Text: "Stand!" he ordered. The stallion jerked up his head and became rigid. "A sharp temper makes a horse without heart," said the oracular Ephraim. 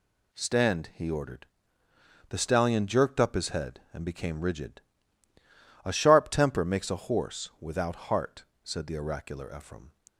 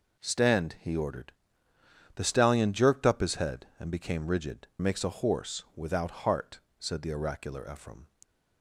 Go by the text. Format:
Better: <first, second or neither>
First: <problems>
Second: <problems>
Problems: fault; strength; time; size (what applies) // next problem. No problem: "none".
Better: first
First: none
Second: skips "A sharp temper"; at 4.7 s